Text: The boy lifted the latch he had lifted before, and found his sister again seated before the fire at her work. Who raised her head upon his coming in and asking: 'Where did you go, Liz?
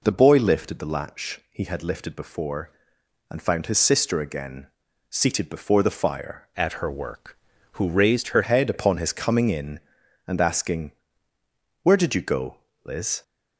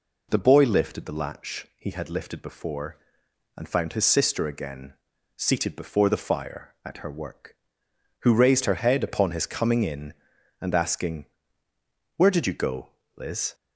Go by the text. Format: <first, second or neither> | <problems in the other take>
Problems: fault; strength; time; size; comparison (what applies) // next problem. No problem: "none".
second | pauses between "again" and "seated"; at 4.6 s; 0.42 s long; also in the second // changes voice from "at" to "her"; from 6.5 to 8.4 s; 1.9 s long